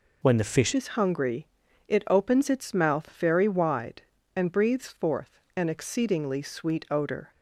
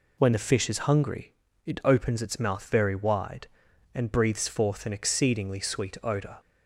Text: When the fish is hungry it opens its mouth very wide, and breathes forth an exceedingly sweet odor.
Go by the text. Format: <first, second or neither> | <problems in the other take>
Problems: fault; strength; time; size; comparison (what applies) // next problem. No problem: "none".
second | changes voice at "is"; from 0.7 s on; 6.6 s long // pauses between "hungry" and "it"; at 1.4 s; 0.40 s long; slight in the second // pauses between "forth" and "an"; slight; at 5.3 s; 0.16 s long